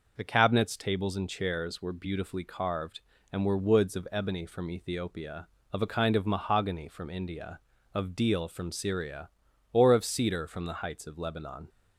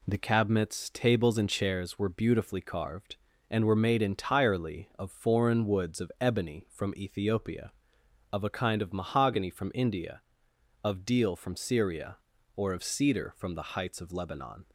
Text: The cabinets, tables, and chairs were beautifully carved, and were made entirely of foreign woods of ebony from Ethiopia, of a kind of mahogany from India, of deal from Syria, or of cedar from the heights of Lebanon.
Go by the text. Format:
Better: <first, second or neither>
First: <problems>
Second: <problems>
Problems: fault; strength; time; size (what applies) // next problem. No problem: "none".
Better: second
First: skips "made entirely of foreign"; at 3.5 s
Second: none